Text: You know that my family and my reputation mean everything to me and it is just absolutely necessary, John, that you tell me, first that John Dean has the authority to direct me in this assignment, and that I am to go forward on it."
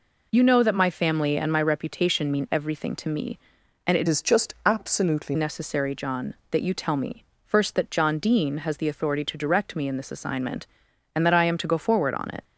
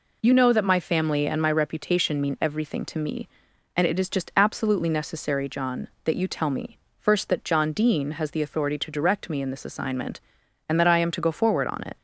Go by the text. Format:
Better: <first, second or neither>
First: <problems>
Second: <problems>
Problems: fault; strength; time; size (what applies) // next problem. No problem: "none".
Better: second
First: changes voice from "is" to "absolutely"; from 4.0 to 5.3 s; 1.3 s long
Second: none